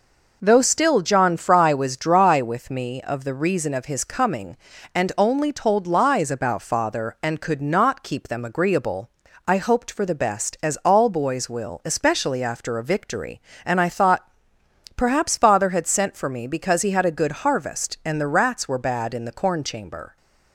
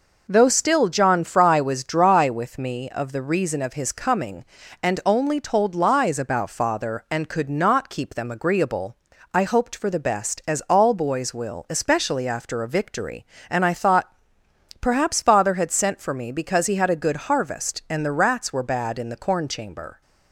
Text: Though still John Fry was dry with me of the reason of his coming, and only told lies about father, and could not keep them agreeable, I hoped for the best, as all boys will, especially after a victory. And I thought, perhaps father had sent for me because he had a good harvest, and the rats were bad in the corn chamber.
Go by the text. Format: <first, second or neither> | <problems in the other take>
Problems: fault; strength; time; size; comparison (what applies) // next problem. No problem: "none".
neither | none